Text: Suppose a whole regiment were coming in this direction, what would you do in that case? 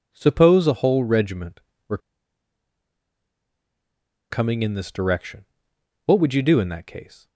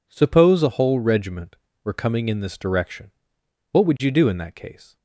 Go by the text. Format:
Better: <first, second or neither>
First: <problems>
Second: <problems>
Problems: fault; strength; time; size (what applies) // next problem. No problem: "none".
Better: second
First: pauses between "were" and "coming"; strong; at 1.9 s; 2.3 s long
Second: none